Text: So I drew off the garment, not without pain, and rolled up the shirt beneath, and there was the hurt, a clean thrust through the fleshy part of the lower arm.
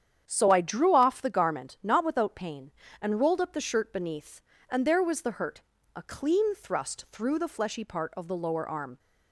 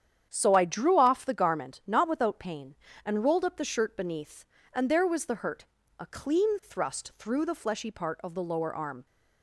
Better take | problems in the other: neither | starts louder than the rest; strong; the same in both

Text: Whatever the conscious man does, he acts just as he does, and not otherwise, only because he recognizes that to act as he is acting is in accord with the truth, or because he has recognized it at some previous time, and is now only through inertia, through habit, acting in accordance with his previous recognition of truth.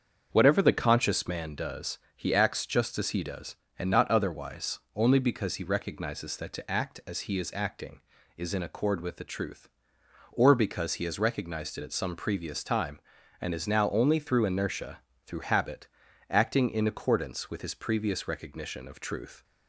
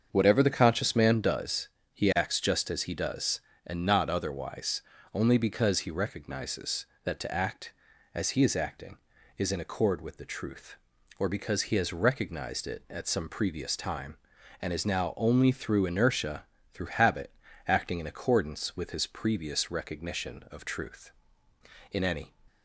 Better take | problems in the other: first | starts louder than the rest; until 1.1 s; 7 dB; also in the first // goes on to say "In any"; slight; from 21.9 s on; 0.44 s long

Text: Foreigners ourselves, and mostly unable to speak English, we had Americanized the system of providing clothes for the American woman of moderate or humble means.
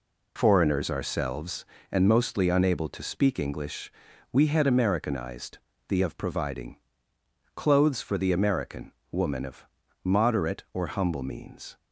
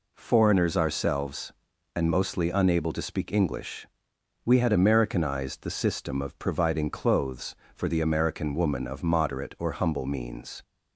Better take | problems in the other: second | pauses between "Americanized" and "the"; slight; at 5.5 s; 0.32 s long // skips "system"; at 6.0 s // pauses between "providing" and "clothes"; noticeable; at 6.7 s; 0.78 s long // pauses between "American" and "woman"; slight; at 8.9 s; 0.20 s long // pauses between "of" and "moderate"; at 9.6 s; 0.40 s long

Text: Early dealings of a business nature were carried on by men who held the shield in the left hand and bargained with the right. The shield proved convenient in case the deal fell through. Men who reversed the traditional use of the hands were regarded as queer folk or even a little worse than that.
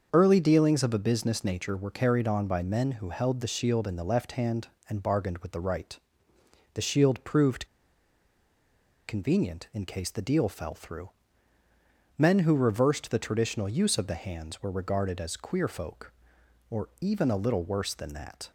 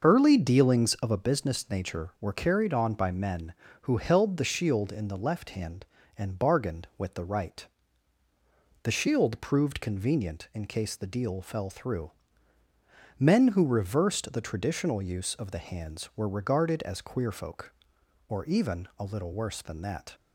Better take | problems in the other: second | starts louder than the rest; until 1.1 s; 6.5 dB; also in the second // pauses between "proved" and "convenient"; strong; at 7.6 s; 1.4 s long

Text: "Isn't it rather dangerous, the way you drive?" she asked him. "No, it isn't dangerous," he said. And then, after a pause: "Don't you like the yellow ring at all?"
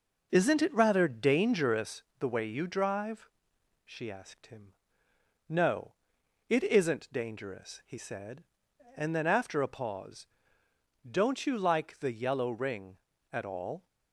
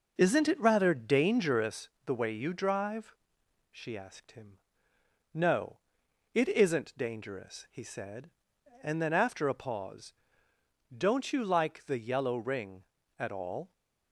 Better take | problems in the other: neither | none

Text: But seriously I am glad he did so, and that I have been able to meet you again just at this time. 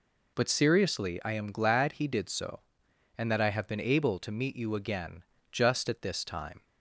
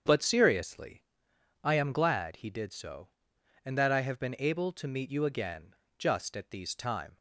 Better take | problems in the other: first | starts louder than the rest; strong; until 1.6 s; 7.5 dB // pauses between "seriously" and "I"; noticeable; at 1.0 s; 0.62 s long // pauses between "again" and "just"; slight; at 5.7 s; 0.24 s long; slight in the first // says "these" for "this"; at 6.5 s

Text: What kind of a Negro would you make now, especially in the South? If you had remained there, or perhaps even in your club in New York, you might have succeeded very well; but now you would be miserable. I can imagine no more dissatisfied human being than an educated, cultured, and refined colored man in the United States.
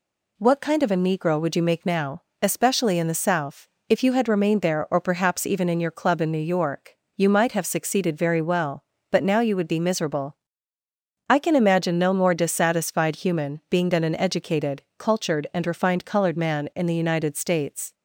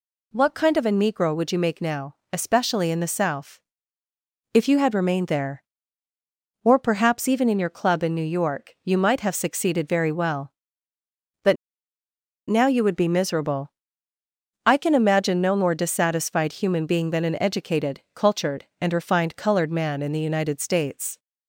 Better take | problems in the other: first | pauses between "but" and "now"; noticeable; at 11.5 s; 0.93 s long

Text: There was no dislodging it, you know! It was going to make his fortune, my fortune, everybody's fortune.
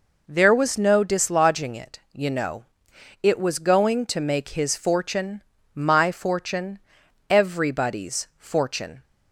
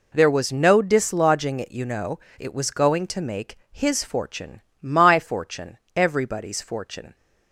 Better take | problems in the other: neither | none

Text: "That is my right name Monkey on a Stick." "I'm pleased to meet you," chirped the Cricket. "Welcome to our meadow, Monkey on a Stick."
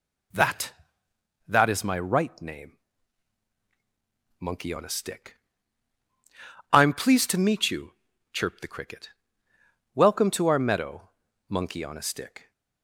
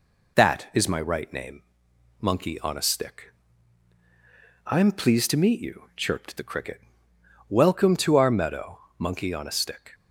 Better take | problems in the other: second | says "That" twice; at 1.4 s // pauses between "name" and "Monkey"; strong; at 2.7 s; 1.6 s long; noticeable in the second

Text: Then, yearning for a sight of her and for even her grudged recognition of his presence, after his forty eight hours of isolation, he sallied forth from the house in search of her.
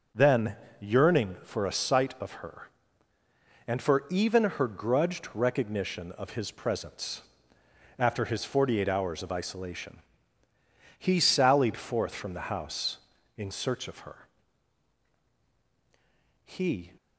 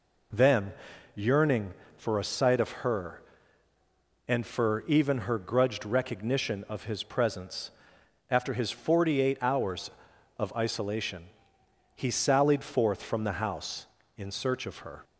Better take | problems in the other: second | goes on to say "He"; slight; from 16.4 s on; 0.46 s long

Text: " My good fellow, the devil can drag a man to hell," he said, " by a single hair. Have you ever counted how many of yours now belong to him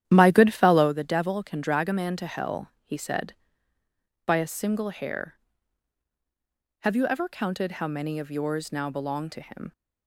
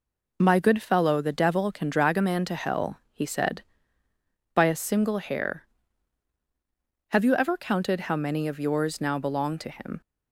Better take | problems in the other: second | starts louder than the rest; strong; until 1.0 s; 11.5 dB

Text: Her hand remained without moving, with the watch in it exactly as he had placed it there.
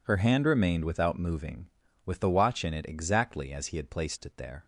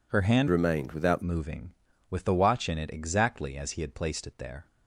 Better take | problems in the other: first | changes voice from "remained" to "without"; from 0.4 to 1.2 s; 0.8 s long

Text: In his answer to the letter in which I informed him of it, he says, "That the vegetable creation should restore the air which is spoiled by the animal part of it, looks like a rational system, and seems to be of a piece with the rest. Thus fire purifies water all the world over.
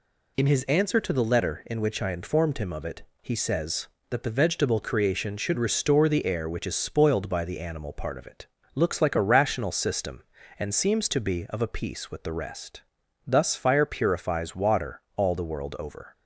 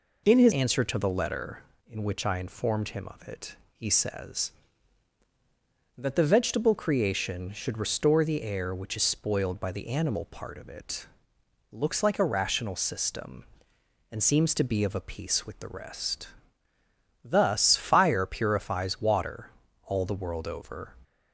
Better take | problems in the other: first | changes voice at "answer"; from 0.5 s on; 20.4 s long // pauses between "water" and "all"; slight; at 19.4 s; 0.36 s long

